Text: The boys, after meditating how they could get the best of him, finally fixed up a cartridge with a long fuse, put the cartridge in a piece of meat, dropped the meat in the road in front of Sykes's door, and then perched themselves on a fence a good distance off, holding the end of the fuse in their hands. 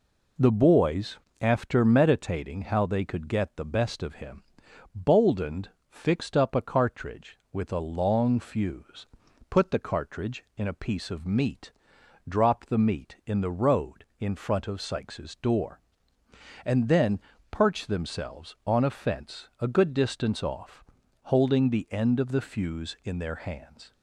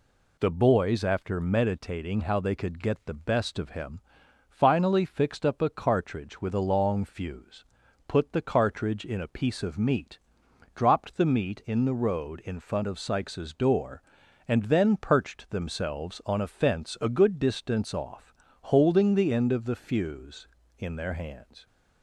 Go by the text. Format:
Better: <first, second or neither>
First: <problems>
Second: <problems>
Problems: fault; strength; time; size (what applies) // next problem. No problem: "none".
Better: second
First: says "boldened" for "finally"; at 4.9 s // pauses between "then" and "perched"; slight; at 17.1 s; 0.32 s long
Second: none